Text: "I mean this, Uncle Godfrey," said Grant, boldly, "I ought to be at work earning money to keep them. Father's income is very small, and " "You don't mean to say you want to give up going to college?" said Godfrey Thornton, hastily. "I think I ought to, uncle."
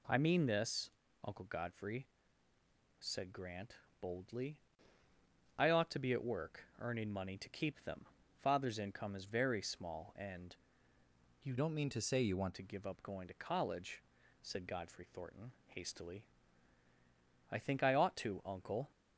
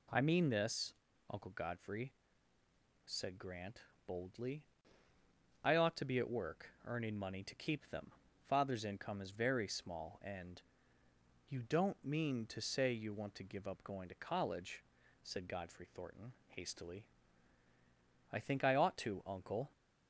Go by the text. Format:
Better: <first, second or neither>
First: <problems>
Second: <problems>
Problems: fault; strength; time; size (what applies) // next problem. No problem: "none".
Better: second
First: changes voice from "don't" to "want"; from 11.5 to 12.5 s; 1.0 s long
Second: none